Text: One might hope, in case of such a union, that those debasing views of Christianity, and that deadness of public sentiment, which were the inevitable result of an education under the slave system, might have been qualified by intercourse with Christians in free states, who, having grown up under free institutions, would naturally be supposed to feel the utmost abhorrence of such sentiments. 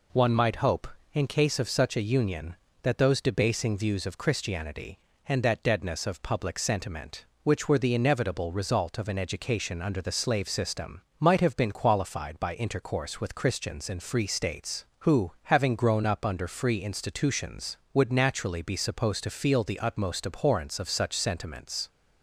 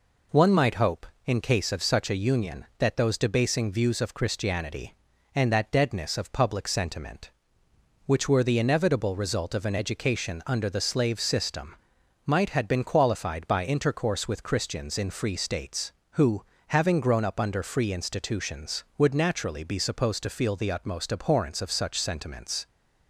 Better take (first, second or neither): first